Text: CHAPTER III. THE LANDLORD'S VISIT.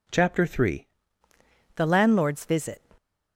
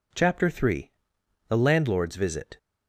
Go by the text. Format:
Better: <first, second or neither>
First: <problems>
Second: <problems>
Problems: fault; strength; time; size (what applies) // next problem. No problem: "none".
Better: second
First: changes voice at "THE"; from 1.7 s on; 1.1 s long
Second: none